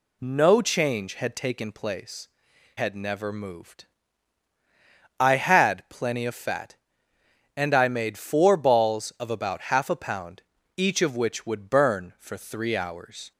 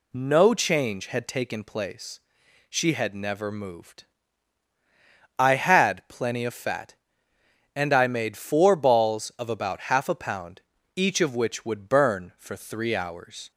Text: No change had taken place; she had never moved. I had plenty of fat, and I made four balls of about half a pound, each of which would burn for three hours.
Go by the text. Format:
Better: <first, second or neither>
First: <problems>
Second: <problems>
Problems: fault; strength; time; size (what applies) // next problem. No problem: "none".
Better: second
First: skips "she"; at 2.5 s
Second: none